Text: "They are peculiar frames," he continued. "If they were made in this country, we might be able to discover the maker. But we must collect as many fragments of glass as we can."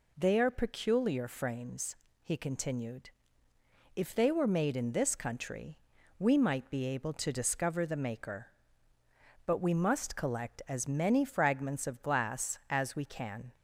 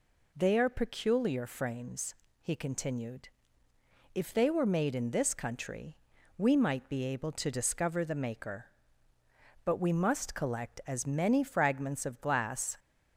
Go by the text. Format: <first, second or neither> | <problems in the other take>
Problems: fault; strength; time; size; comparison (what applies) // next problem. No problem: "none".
first | stops before "as we can"; at 12.7 s